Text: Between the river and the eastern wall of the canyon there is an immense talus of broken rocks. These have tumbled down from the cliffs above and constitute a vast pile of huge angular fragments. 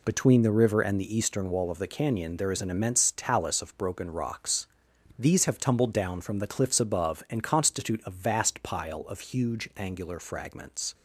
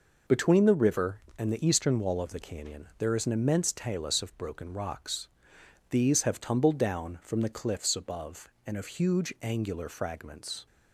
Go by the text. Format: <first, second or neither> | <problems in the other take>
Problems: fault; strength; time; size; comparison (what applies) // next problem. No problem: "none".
first | skips "constitute a vast pile"; at 8.7 s